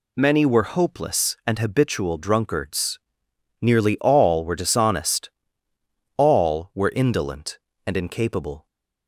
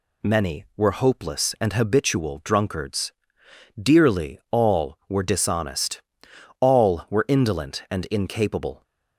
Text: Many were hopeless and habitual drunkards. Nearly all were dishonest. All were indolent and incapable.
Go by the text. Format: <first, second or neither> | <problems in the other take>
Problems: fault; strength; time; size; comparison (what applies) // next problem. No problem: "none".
first | says "Dearly" for "Nearly"; at 3.8 s